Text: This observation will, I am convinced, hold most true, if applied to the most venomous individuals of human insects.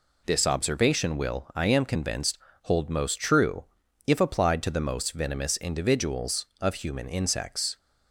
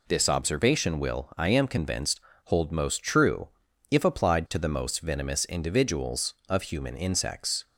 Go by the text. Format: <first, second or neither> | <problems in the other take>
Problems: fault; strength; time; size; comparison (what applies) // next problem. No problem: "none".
neither | none